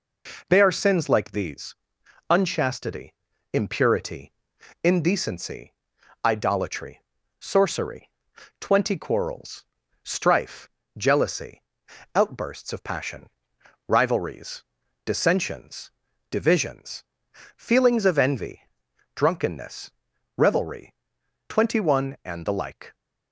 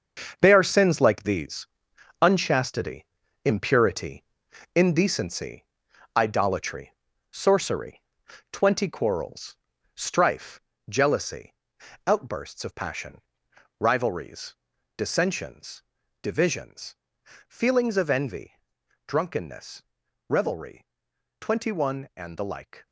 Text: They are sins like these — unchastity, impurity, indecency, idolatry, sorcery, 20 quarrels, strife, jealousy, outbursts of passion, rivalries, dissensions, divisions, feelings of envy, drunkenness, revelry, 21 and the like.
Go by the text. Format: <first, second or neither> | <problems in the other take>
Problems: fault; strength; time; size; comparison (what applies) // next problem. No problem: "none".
first | gets quieter; strong; throughout; 10 dB